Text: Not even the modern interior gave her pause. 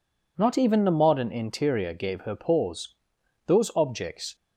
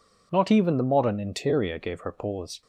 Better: second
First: goes on to say "Those objects"; noticeable; from 3.4 s on; 0.88 s long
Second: none

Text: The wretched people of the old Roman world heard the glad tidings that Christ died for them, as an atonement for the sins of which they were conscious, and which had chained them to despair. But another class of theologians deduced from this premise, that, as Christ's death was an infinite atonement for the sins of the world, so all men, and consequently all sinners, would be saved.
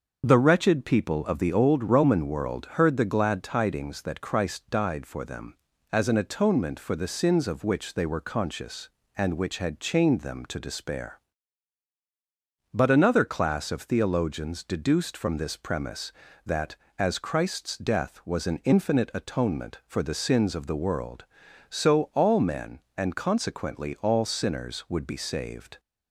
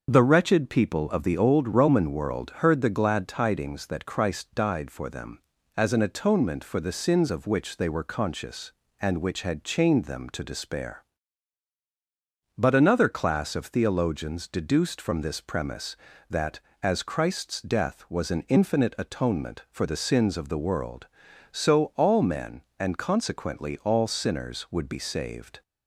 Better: neither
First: starts louder than the rest; until 1.2 s; 6.5 dB // pauses between "world" and "heard"; slight; at 2.6 s; 0.16 s long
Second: starts louder than the rest; until 1.1 s; 6.5 dB // pauses between "world" and "heard"; slight; at 2.4 s; 0.16 s long

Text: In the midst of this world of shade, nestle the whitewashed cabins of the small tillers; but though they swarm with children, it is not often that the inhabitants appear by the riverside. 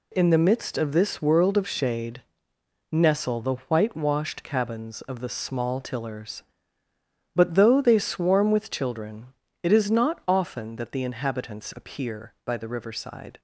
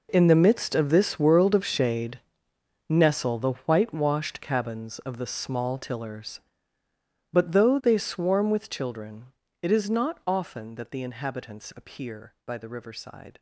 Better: first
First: none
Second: gets quieter; strong; throughout; 15.5 dB

